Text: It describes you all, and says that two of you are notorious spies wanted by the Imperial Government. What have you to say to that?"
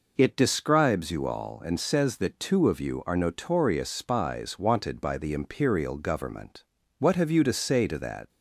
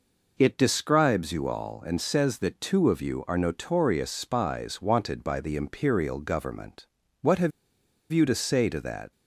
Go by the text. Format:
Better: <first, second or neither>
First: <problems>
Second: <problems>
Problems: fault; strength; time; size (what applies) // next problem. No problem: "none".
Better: first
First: none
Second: pauses between "have" and "you"; noticeable; at 7.5 s; 0.62 s long